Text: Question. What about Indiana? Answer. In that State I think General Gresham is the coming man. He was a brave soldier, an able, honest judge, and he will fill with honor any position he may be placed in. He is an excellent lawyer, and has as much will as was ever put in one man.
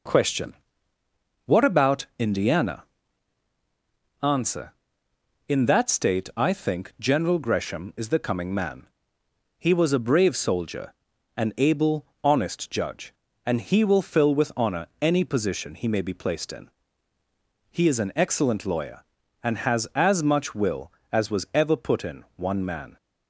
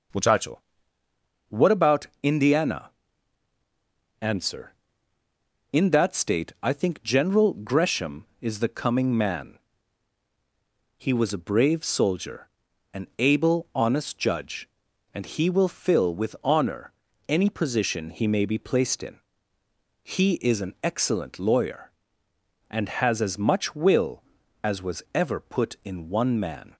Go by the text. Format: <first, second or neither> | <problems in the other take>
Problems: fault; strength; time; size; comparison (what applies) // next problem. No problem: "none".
first | says "Muchacho" for "Question"; at 0.1 s // pauses between "honor" and "any"; at 16.9 s; 0.38 s long